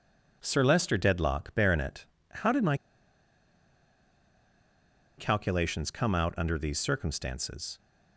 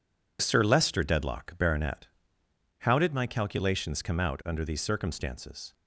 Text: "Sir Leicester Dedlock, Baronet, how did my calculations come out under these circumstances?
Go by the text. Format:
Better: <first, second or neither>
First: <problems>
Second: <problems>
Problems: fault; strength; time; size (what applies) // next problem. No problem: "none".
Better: second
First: pauses between "my" and "calculations"; strong; at 2.7 s; 2.3 s long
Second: none